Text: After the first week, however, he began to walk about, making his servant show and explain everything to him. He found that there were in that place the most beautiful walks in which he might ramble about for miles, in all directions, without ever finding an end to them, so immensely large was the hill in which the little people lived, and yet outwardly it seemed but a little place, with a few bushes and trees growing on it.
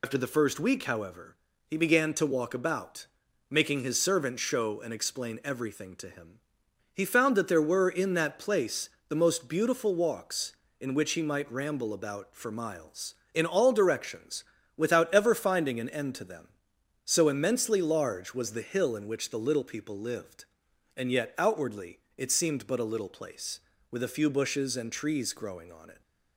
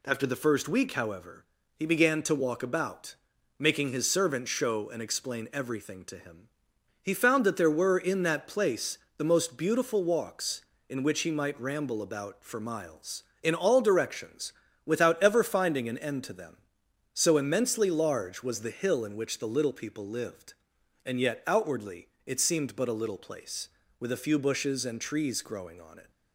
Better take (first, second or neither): second